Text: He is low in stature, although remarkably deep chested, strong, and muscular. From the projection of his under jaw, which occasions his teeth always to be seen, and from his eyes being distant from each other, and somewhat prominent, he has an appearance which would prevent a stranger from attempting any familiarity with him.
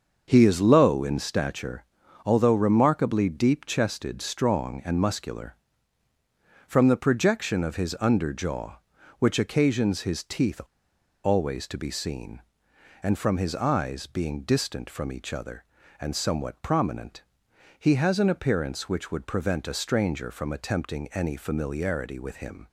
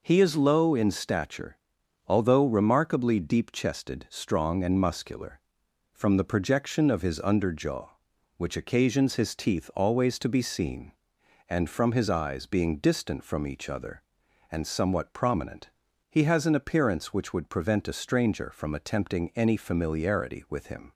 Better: second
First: starts louder than the rest; until 1.2 s; 6 dB // pauses between "teeth" and "always"; noticeable; at 10.6 s; 0.63 s long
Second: none

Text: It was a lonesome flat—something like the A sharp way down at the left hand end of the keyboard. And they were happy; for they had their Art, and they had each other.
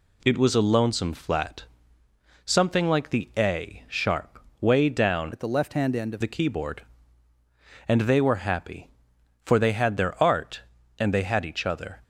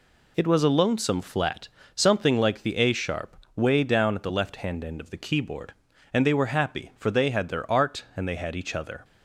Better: second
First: pauses between "sharp" and "way"; slight; at 4.3 s; 0.22 s long // changes voice from "at" to "of"; from 5.3 to 6.2 s; 0.9 s long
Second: pauses between "sharp" and "way"; slight; at 3.3 s; 0.18 s long

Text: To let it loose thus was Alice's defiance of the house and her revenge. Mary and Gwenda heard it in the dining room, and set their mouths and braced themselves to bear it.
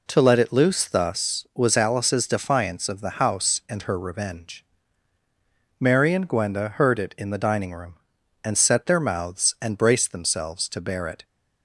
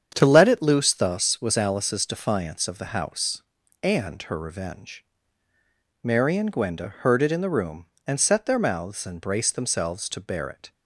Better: first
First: none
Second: starts louder than the rest; strong; until 1.1 s; 8 dB // skips "dining"; at 7.4 s

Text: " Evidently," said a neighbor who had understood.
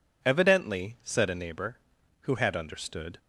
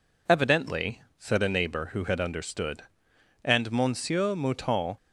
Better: first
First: none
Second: goes on to say "And Monsieur Mouton"; from 3.4 s on; 1.5 s long

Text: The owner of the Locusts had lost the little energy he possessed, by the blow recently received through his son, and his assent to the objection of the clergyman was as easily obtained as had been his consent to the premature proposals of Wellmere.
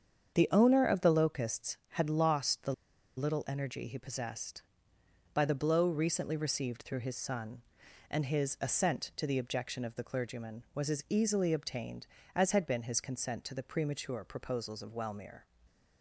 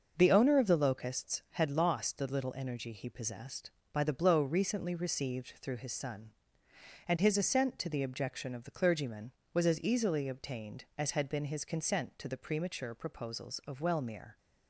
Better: second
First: starts louder than the rest; strong; until 1.4 s; 7.5 dB // pauses between "the" and "little"; at 2.7 s; 0.44 s long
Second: starts louder than the rest; until 1.1 s; 6 dB

